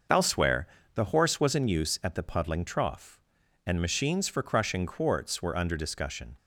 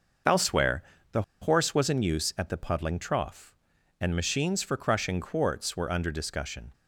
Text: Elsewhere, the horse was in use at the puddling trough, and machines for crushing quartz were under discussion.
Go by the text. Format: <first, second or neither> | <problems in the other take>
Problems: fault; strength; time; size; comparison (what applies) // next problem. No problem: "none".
first | pauses between "the" and "horse"; slight; at 1.2 s; 0.18 s long